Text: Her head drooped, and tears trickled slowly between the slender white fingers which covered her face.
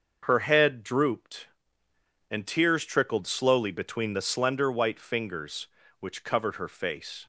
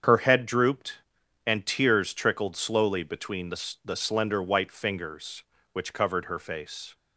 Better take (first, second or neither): first